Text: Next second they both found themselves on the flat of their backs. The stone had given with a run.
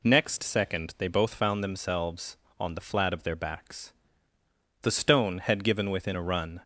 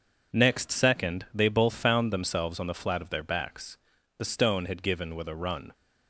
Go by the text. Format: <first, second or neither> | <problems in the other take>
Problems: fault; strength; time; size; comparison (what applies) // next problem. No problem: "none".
second | says "within" for "with"; at 5.8 s